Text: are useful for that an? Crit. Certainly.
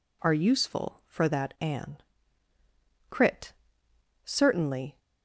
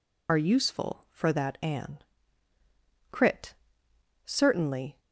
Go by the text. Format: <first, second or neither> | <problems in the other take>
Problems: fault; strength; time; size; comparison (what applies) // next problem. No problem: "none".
first | loses the start of "are"; at 0.2 s; 45 ms